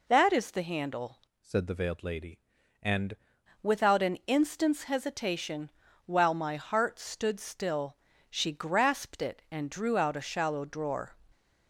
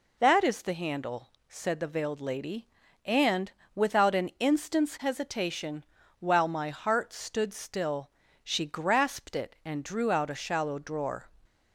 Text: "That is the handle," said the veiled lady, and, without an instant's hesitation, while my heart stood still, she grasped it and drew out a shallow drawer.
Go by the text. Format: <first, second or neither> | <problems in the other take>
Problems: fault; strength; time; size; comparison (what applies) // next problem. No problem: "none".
second | changes voice from "said" to "and"; from 1.4 to 3.1 s; 1.7 s long